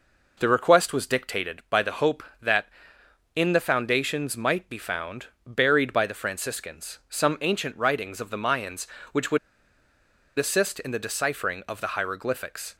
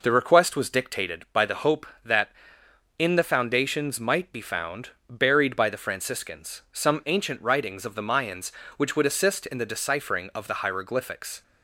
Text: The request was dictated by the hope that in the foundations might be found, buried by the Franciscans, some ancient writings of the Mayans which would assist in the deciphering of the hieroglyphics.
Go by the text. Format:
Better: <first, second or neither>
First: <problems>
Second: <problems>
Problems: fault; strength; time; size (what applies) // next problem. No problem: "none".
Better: second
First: pauses between "would" and "assist"; at 9.3 s; 1.0 s long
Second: none